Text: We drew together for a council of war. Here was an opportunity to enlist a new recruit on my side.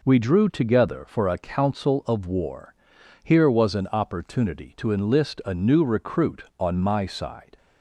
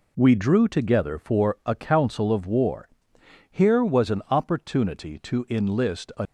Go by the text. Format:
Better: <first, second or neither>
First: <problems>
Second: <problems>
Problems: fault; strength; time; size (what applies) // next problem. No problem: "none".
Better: first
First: none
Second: stops before "new recruit on my side"; at 6.2 s